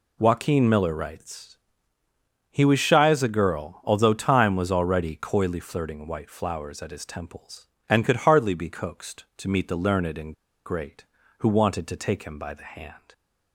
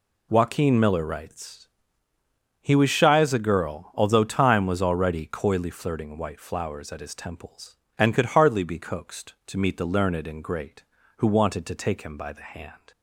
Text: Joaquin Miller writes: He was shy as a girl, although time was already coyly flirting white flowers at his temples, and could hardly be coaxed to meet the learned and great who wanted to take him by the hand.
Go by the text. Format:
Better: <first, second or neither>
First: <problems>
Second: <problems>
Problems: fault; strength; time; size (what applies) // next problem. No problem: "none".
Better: second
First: pauses between "and" and "great"; slight; at 10.3 s; 0.31 s long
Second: none